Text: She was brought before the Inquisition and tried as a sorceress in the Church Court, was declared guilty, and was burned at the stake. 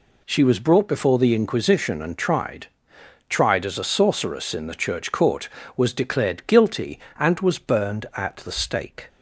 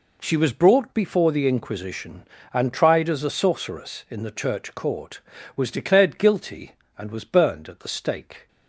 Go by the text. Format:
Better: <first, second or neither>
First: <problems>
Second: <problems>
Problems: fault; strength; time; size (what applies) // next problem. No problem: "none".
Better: second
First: says "tried" twice; at 3.2 s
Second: none